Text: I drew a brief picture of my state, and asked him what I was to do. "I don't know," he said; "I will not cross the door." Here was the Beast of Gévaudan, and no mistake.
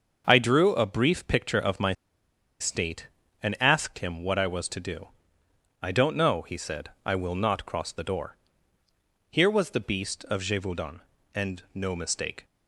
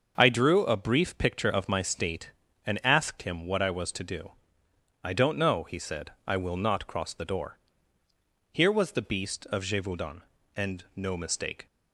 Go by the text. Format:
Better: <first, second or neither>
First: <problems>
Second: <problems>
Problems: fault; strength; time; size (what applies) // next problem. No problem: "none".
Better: second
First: starts louder than the rest; until 1.2 s; 6.5 dB // pauses between "my" and "state"; noticeable; at 1.9 s; 0.66 s long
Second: starts louder than the rest; until 1.1 s; 6.5 dB